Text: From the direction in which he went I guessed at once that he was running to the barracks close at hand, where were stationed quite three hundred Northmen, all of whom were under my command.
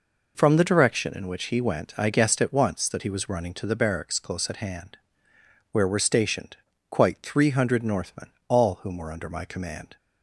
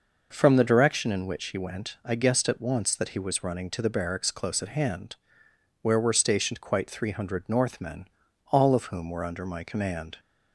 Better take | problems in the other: second | pauses between "stationed" and "quite"; slight; at 6.5 s; 0.32 s long // skips "of"; at 8.7 s

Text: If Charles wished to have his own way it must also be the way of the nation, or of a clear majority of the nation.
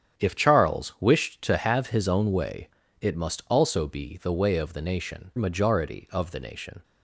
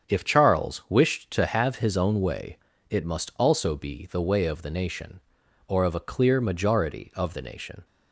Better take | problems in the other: second | starts louder than the rest; strong; until 1.2 s; 9 dB; strong in the second // pauses between "way" and "it"; slight; at 2.6 s; 0.32 s long; slight in the second // skips "or of a clear"; at 5.3 s

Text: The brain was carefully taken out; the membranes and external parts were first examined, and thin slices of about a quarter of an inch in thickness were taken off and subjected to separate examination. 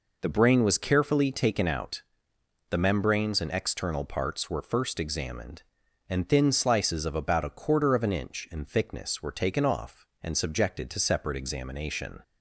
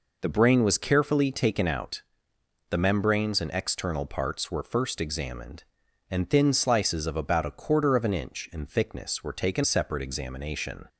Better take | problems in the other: first | skips "off and subjected to"; at 9.6 s

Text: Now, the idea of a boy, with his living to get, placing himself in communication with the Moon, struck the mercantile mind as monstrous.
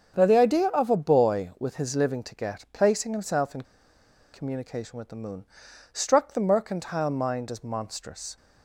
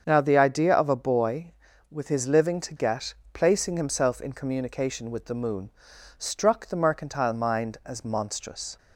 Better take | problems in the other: second | starts louder than the rest; until 1.1 s; 7 dB; also in the second // pauses between "in" and "communication"; noticeable; at 3.6 s; 0.70 s long

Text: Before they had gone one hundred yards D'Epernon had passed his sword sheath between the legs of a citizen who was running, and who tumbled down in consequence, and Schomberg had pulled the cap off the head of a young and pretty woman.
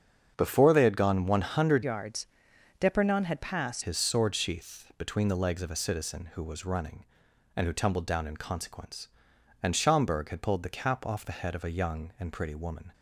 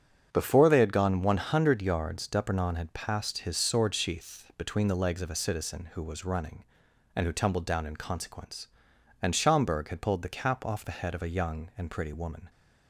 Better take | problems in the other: second | starts louder than the rest; strong; until 1.3 s; 7 dB; strong in the second // changes voice from "yards" to "passed"; from 1.8 to 3.8 s; 2.0 s long // pauses between "yards" and "D'Epernon"; noticeable; at 2.2 s; 0.54 s long

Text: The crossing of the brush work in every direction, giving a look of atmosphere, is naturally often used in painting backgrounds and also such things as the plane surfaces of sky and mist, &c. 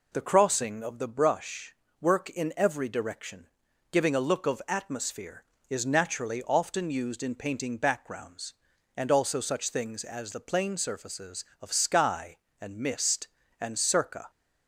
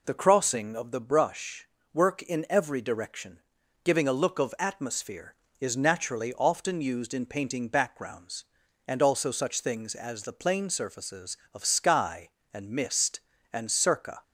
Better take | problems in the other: neither | pauses between "brush" and "work"; slight; the same in both

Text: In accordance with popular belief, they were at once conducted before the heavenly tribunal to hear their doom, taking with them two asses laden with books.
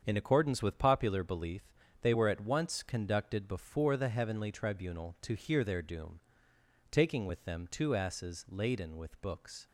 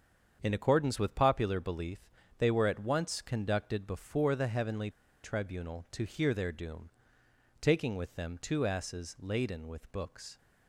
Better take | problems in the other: first | starts louder than the rest; strong; until 1.4 s; 7.5 dB; strong in the first // pauses between "heavenly" and "tribunal"; slight; at 4.8 s; 0.33 s long

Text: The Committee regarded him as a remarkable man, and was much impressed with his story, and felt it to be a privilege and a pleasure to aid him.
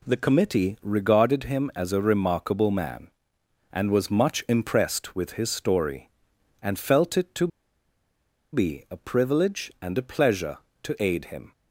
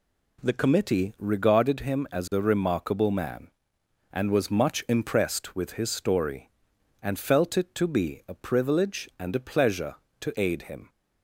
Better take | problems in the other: second | pauses between "to" and "be"; at 7.4 s; 1.0 s long

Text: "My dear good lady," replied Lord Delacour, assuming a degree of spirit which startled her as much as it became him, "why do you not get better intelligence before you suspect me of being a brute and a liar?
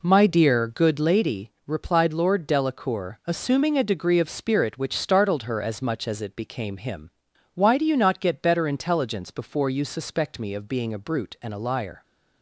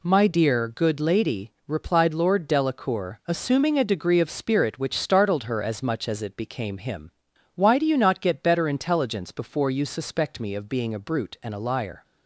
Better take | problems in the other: second | starts louder than the rest; until 1.3 s; 3.5 dB

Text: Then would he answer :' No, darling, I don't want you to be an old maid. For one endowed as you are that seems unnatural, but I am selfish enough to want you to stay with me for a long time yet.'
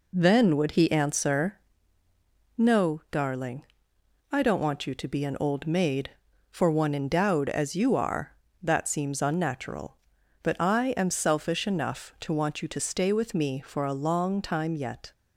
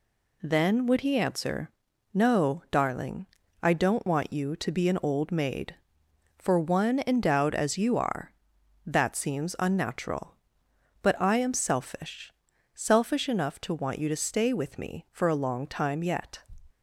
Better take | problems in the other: first | says "selfish" twice; at 12.7 s

